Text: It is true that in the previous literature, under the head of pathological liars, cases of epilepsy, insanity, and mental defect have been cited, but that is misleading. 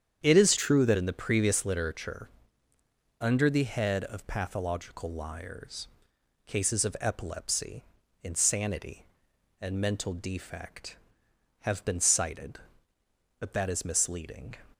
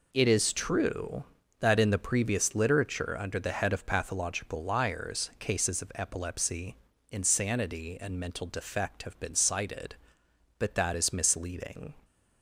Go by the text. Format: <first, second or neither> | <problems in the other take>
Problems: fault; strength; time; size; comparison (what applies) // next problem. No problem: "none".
second | starts louder than the rest; strong; until 1.2 s; 8.5 dB // changes voice from "true" to "that"; from 0.5 to 0.9 s; 0.4 s long